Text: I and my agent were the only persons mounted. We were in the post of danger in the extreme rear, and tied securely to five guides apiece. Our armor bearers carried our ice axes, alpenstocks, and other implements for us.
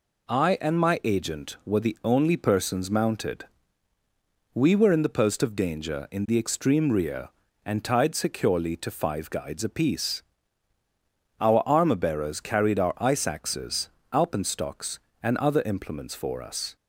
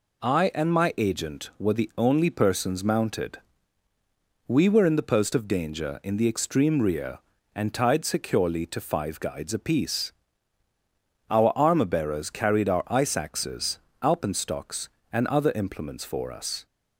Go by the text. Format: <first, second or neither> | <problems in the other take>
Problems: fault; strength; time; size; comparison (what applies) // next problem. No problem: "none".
neither | none